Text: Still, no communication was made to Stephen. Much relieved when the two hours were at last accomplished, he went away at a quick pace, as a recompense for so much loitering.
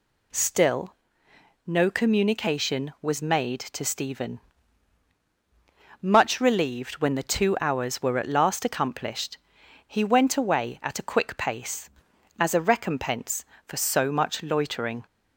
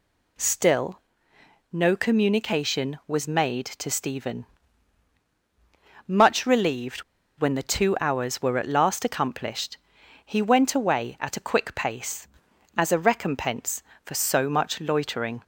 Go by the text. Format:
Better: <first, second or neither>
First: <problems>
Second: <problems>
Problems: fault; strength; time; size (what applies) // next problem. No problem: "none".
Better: first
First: none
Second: pauses between "relieved" and "when"; slight; at 7.0 s; 0.34 s long